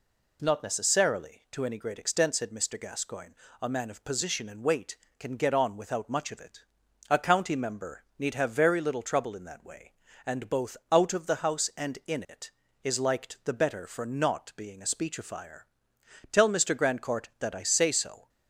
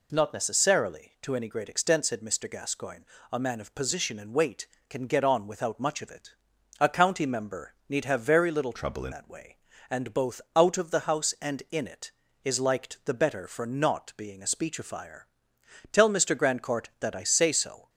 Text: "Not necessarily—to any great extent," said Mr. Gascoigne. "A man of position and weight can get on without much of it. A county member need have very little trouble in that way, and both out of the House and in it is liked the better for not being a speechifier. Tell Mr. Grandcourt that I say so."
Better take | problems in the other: first | changes voice from "trouble" to "in"; from 8.7 to 9.1 s; 0.4 s long

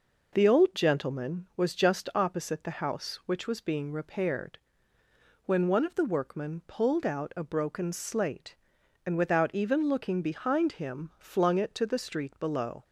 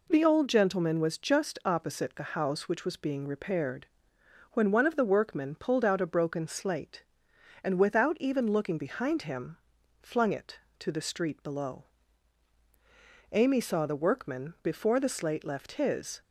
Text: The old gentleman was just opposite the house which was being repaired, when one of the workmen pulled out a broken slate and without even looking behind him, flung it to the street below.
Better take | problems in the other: first | goes on to say "Amy saw the workman before the slate left his"; strong; from 13.3 s on; 2.8 s long

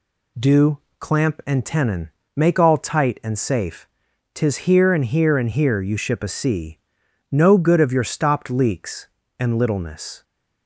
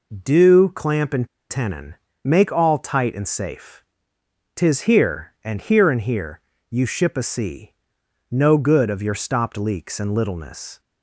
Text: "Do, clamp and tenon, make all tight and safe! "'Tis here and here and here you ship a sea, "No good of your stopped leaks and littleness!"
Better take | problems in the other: first | pauses between "and" and "tenon"; slight; at 1.2 s; 0.22 s long // pauses between "here" and "you"; slight; at 6.3 s; 0.28 s long

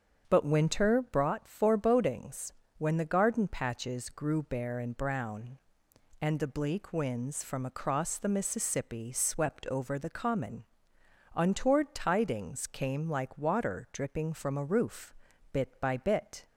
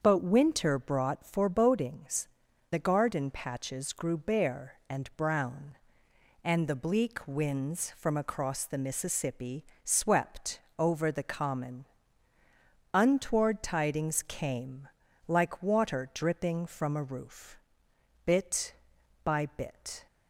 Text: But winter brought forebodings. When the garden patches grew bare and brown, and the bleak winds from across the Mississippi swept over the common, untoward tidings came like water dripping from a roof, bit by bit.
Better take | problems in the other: first | starts louder than the rest; until 1.0 s; 7 dB; strong in the first // skips "When"; at 2.4 s // pauses between "Mississippi" and "swept"; slight; at 9.6 s; 0.20 s long // pauses between "swept" and "over"; slight; at 10.6 s; 0.18 s long // pauses between "came" and "like"; at 14.8 s; 0.38 s long

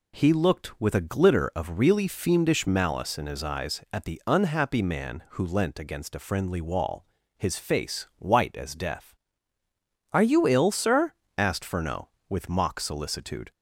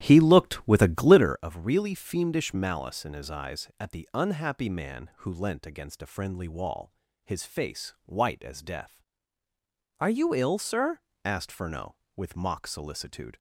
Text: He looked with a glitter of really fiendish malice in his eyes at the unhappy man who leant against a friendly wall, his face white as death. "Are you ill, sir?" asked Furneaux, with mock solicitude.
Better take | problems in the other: first | starts louder than the rest; strong; until 1.4 s; 11.5 dB

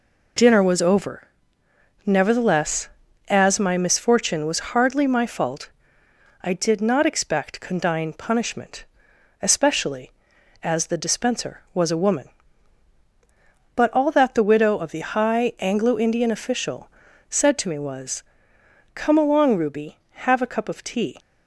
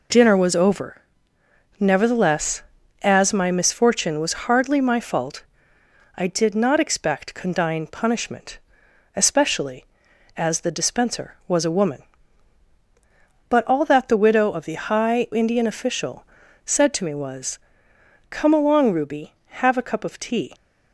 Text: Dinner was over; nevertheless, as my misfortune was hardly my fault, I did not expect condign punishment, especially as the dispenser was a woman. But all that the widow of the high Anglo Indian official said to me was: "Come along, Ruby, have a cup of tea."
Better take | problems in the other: first | skips "Anglo"; at 15.2 s // pauses between "official" and "said"; at 16.2 s; 0.40 s long; also in the first

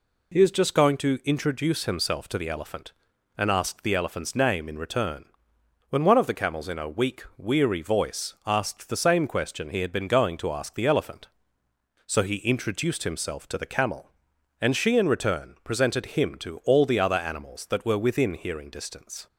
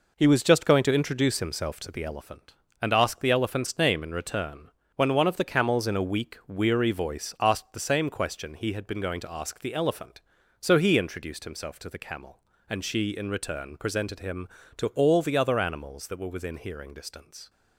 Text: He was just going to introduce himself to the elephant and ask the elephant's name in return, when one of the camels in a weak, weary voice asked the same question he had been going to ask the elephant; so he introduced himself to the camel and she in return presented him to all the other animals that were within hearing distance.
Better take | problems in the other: second | says "is" for "was"; at 0.4 s

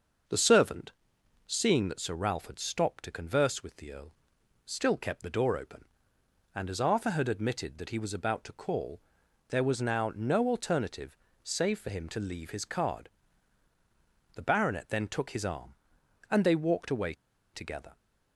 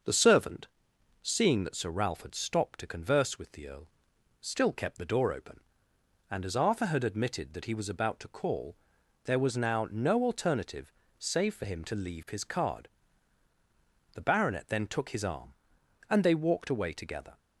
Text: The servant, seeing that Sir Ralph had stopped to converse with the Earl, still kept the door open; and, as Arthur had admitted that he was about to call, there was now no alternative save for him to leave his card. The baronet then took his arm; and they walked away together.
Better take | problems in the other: second | starts louder than the rest; until 1.8 s; 6.5 dB; also in the second // pauses between "alternative" and "save"; slight; at 11.1 s; 0.28 s long; slight in the second // pauses between "away" and "together"; at 17.1 s; 0.39 s long

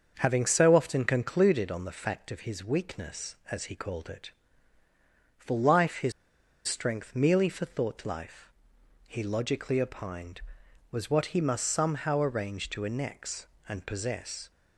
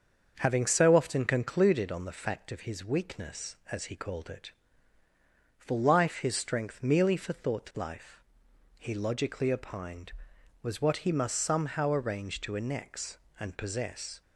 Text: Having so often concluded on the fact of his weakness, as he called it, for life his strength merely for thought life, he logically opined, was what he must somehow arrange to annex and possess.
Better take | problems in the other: second | starts louder than the rest; until 1.2 s; 6.5 dB; also in the second // pauses between "his" and "strength"; noticeable; at 6.1 s; 0.55 s long

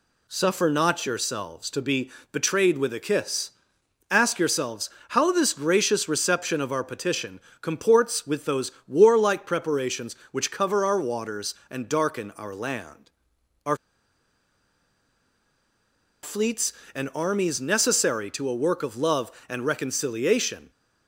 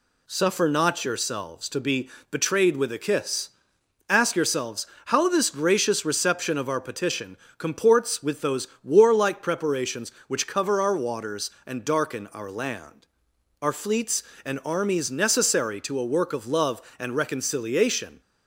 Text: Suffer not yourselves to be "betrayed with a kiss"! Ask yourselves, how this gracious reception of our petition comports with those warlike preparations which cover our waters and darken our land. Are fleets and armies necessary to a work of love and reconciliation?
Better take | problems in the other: second | pauses between "be" and "betrayed"; slight; at 2.1 s; 0.22 s long; slight in the second // pauses between "petition" and "comports"; slight; at 7.4 s; 0.22 s long; slight in the second // pauses between "those" and "warlike"; slight; at 8.7 s; 0.16 s long; slight in the second // pauses between "Are" and "fleets"; strong; at 13.7 s; 2.4 s long

